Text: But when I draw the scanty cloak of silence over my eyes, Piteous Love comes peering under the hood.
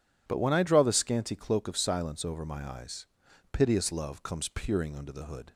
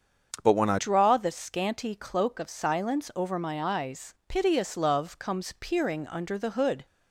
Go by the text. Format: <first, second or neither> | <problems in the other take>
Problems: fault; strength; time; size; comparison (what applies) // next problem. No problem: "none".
first | starts louder than the rest; until 1.4 s; 7 dB // changes voice at "draw"; from 0.7 s on; 6.1 s long